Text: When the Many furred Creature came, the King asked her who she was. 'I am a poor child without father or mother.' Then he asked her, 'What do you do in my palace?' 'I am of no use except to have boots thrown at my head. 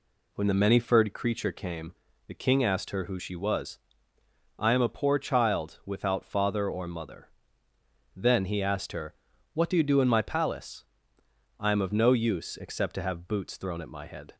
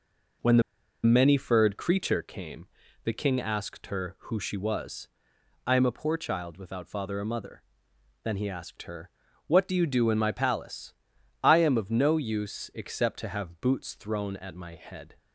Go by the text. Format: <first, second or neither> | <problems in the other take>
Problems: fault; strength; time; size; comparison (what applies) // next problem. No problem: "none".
first | pauses between "the" and "Many"; at 0.6 s; 0.42 s long